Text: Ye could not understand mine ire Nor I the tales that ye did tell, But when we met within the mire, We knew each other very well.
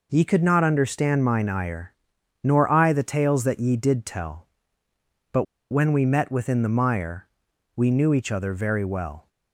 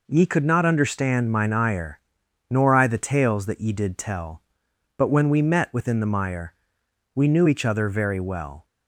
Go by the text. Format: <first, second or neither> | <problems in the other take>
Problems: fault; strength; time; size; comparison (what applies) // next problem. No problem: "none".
second | pauses between "ire" and "Nor"; noticeable; at 1.9 s; 0.48 s long; noticeable in the second // pauses between "But" and "when"; slight; at 5.4 s; 0.27 s long